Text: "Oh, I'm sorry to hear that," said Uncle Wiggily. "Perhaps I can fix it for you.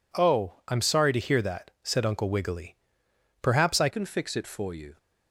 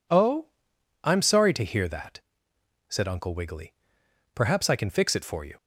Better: second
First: changes voice at "can"; from 3.9 s on; 1.0 s long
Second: none

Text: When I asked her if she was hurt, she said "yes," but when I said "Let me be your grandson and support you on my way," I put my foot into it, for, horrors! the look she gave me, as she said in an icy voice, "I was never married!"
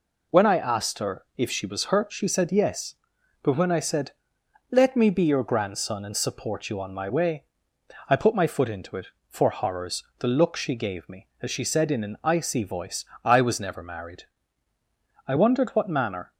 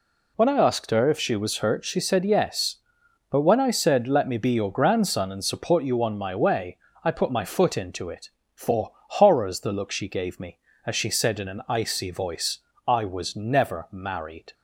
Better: second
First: pauses between "said" and "Let"; noticeable; at 4.1 s; 0.60 s long // goes on to say "I wondered what manner"; noticeable; from 15.2 s on; 1.0 s long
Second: none

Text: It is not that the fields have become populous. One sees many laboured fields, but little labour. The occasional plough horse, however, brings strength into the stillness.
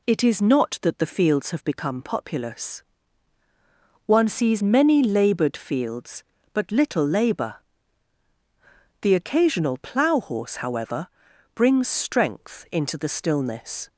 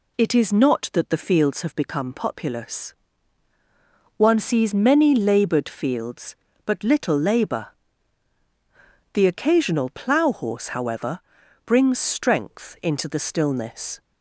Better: neither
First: none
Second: none

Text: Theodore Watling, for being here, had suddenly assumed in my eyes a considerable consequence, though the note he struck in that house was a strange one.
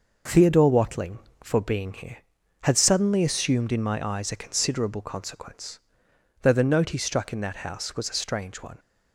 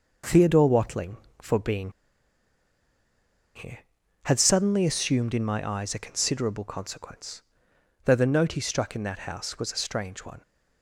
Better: first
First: none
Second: pauses between "being" and "here"; strong; at 1.9 s; 1.6 s long

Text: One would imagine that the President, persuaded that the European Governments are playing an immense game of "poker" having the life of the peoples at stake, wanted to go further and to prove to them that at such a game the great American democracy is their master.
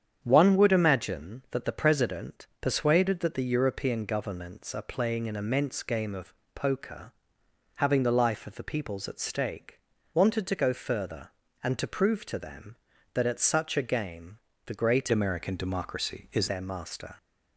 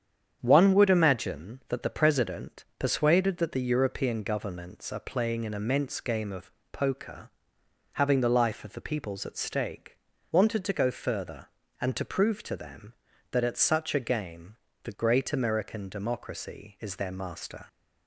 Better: second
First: starts louder than the rest; strong; until 1.2 s; 8 dB // pauses between "of" and "poker"; slight; at 6.3 s; 0.22 s long // pauses between "poker" and "having"; noticeable; at 7.1 s; 0.66 s long // pauses between "game" and "the"; slight; at 14.3 s; 0.28 s long // changes voice from "American" to "is"; from 15.1 to 16.4 s; 1.3 s long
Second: starts louder than the rest; strong; until 1.4 s; 8 dB // pauses between "of" and "poker"; slight; at 6.5 s; 0.22 s long // pauses between "poker" and "having"; noticeable; at 7.2 s; 0.66 s long // pauses between "game" and "the"; slight; at 14.5 s; 0.28 s long

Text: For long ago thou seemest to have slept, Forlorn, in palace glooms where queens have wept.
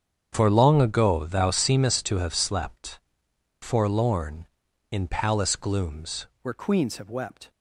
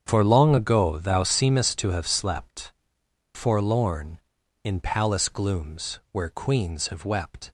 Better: second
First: starts louder than the rest; strong; until 1.3 s; 8 dB // changes voice at "where"; from 6.4 s on; 1.0 s long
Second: starts louder than the rest; strong; until 1.1 s; 8 dB

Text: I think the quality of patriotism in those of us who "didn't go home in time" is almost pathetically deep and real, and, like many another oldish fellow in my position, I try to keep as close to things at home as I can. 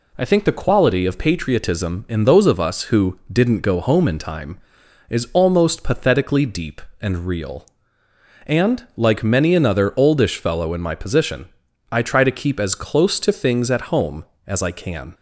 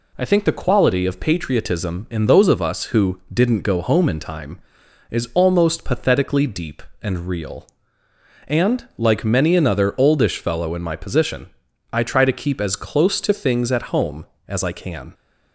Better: neither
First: none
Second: none

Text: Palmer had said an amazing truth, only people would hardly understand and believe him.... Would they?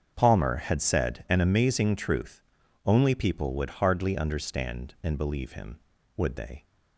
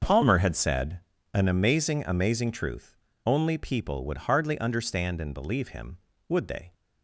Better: first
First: starts louder than the rest; strong; until 1.1 s; 7.5 dB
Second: starts louder than the rest; until 1.3 s; 6.5 dB // pauses between "said" and "an"; slight; at 0.9 s; 0.34 s long // says "amazing" twice; at 2.0 s

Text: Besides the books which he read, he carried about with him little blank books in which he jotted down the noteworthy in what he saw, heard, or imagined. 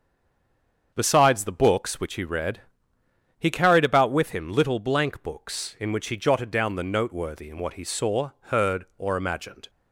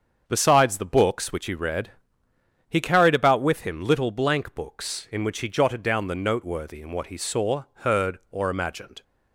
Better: second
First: stays silent before the first word; slight; until 0.9 s; 0.9 s long // starts louder than the rest; until 1.9 s; 7 dB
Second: starts louder than the rest; until 1.2 s; 7 dB

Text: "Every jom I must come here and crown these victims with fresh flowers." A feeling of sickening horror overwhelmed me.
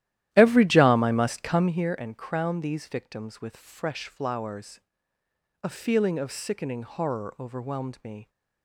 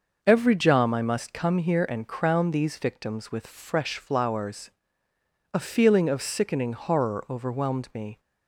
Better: second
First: starts louder than the rest; strong; until 1.9 s; 13 dB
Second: none

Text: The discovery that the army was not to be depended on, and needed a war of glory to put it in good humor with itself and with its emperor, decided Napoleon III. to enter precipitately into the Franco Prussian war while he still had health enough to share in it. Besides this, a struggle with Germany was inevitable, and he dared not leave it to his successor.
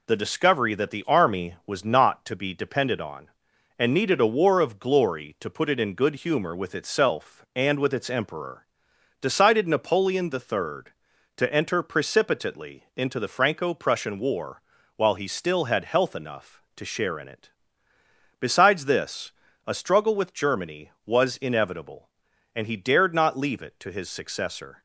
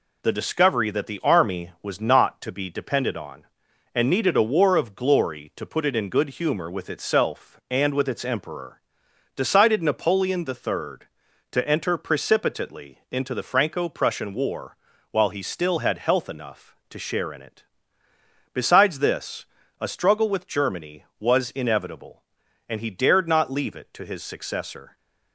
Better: neither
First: pauses between "war" and "while"; slight; at 14.6 s; 0.36 s long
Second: pauses between "war" and "while"; slight; at 14.7 s; 0.36 s long

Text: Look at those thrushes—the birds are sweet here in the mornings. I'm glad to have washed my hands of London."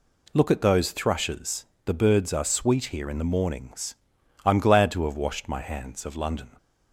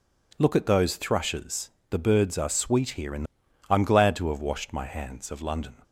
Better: first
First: none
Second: skips "mornings"; at 3.4 s

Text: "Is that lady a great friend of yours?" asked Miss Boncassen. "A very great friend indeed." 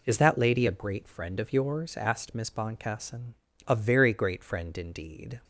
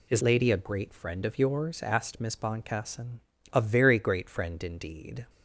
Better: first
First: none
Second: skips "that"; at 0.2 s

